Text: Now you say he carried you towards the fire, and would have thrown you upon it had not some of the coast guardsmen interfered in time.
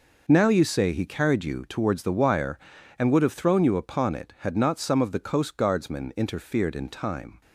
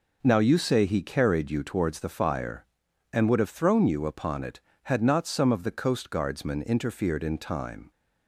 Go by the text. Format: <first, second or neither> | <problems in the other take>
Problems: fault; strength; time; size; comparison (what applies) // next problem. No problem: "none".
second | says "wire" for "fire"; at 2.1 s